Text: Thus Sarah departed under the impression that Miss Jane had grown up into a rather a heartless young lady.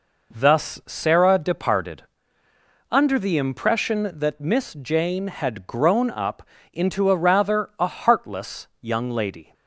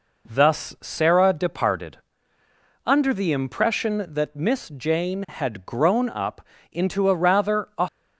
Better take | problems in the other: first | pauses between "departed" and "under"; noticeable; at 1.9 s; 0.86 s long; noticeable in the first // pauses between "up" and "into"; slight; at 6.4 s; 0.30 s long; slight in the first // stops before "heartless young lady"; at 7.8 s

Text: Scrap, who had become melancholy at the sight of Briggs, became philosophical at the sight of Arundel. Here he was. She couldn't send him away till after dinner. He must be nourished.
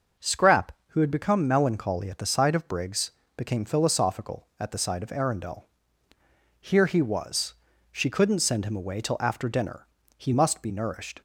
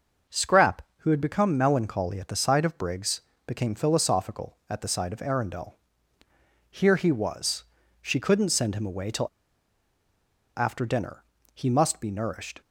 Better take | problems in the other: first | starts louder than the rest; until 1.4 s; 6 dB; also in the first // pauses between "till" and "after"; strong; at 9.2 s; 1.2 s long

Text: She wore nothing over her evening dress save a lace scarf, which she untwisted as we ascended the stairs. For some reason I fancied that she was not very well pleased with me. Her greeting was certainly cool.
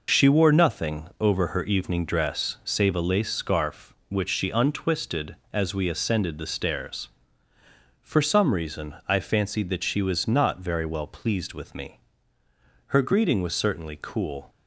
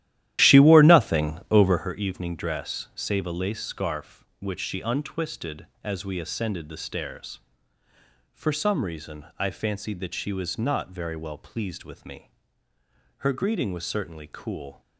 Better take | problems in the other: first | starts louder than the rest; strong; until 1.9 s; 13 dB

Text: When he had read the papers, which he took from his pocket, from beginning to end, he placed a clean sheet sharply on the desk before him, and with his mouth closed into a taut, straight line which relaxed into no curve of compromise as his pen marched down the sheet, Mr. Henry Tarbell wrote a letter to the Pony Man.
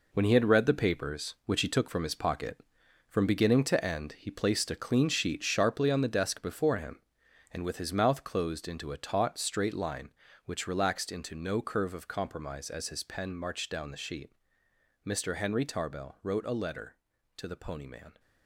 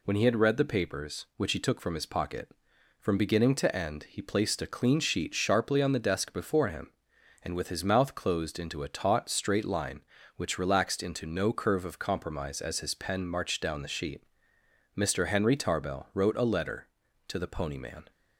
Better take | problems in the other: second | gets quieter; strong; throughout; 8.5 dB

